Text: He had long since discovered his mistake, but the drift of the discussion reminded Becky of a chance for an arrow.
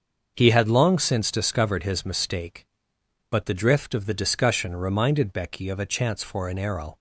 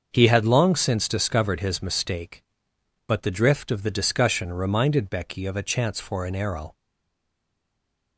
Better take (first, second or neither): first